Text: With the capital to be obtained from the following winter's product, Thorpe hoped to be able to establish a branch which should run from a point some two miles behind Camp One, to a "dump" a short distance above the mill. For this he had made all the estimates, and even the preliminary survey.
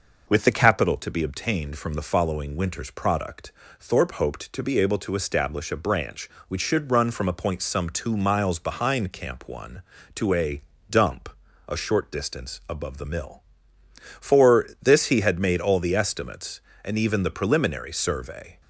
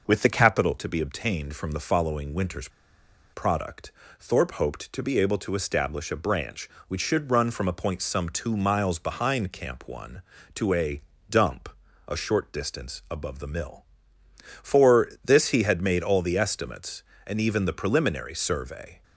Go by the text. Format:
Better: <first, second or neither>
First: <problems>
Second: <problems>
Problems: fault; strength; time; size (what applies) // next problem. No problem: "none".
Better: first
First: pauses between "a" and "dump"; slight; at 10.6 s; 0.30 s long // pauses between "dump" and "a"; at 11.2 s; 0.40 s long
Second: pauses between "winter's" and "product"; noticeable; at 2.6 s; 0.64 s long // pauses between "a" and "dump"; slight; at 11.0 s; 0.30 s long // pauses between "dump" and "a"; at 11.6 s; 0.40 s long